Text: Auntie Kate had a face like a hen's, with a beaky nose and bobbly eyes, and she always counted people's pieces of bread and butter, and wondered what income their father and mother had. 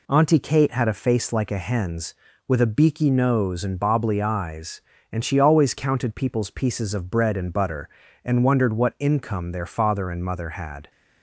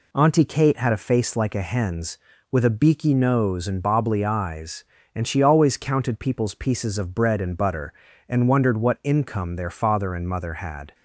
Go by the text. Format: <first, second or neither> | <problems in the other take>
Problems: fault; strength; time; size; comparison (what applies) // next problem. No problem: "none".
neither | none